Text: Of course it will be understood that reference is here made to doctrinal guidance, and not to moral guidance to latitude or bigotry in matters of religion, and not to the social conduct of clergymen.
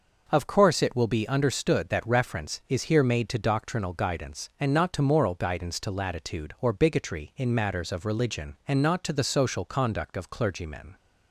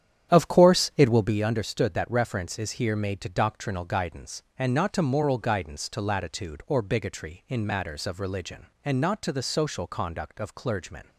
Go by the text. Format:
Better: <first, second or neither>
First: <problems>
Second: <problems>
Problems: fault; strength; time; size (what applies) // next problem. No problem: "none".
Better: first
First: none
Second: starts louder than the rest; strong; until 1.5 s; 9.5 dB